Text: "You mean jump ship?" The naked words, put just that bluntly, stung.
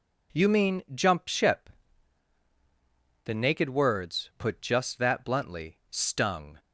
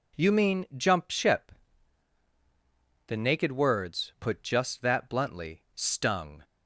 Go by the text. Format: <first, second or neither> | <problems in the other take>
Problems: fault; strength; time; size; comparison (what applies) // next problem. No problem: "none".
neither | none